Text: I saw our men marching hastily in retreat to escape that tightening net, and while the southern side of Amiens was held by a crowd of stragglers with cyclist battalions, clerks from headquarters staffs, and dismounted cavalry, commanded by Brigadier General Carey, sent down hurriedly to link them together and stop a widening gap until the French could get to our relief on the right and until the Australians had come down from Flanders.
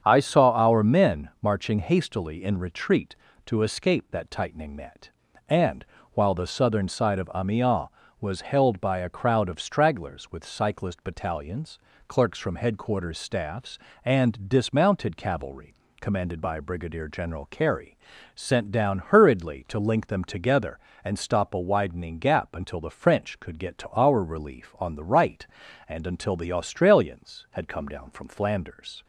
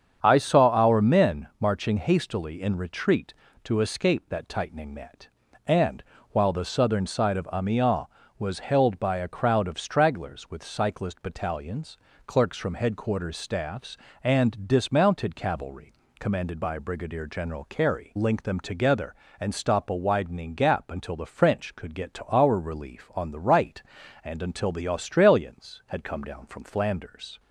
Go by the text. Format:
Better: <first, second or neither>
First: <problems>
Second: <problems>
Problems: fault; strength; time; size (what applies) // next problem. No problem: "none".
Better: first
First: starts louder than the rest; strong; until 1.0 s; 7.5 dB // pauses between "and" and "while"; slight; at 5.8 s; 0.30 s long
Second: starts louder than the rest; strong; until 1.2 s; 7.5 dB // pauses between "and" and "while"; slight; at 6.0 s; 0.30 s long // skips "sent down hurriedly to"; at 18.1 s